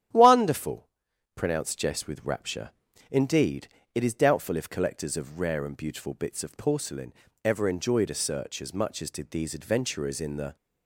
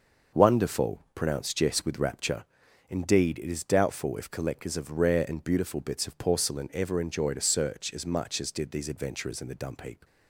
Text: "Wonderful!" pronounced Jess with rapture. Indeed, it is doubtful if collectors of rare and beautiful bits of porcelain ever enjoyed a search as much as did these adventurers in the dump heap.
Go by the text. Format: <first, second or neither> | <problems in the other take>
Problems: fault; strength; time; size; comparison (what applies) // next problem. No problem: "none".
second | starts louder than the rest; strong; until 1.5 s; 10.5 dB; noticeable in the second // pauses between "porcelain" and "ever"; slight; at 7.1 s; 0.32 s long // stops before "dump heap"; at 10.5 s